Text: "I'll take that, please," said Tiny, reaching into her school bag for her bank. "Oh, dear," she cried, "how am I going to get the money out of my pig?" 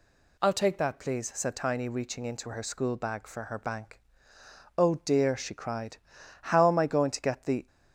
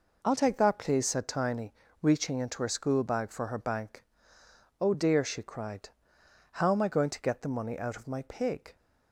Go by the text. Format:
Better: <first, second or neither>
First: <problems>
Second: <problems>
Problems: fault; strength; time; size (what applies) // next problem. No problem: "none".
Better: second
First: stops before "money out of my pig"; at 7.6 s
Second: none